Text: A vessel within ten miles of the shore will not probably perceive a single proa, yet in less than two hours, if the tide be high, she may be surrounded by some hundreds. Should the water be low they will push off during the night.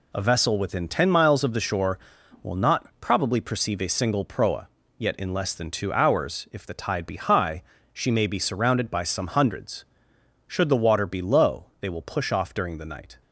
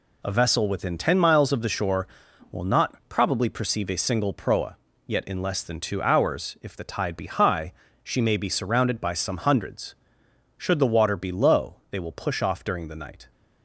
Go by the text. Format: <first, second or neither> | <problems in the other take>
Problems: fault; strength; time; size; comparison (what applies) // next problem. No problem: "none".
neither | none